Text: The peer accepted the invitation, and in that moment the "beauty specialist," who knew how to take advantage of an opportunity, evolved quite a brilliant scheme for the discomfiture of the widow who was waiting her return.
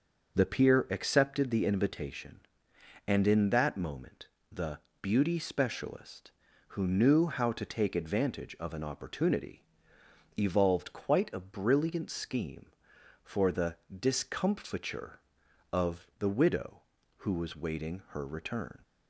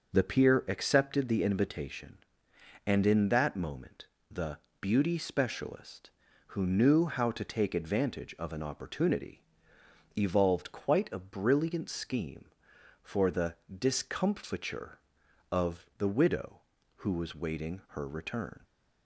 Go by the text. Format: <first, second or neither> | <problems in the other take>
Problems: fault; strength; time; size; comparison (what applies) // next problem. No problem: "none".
neither | pauses between "moment" and "the"; slight; the same in both // pauses between "the" and "beauty"; slight; the same in both // pauses between "the" and "discomfiture"; slight; the same in both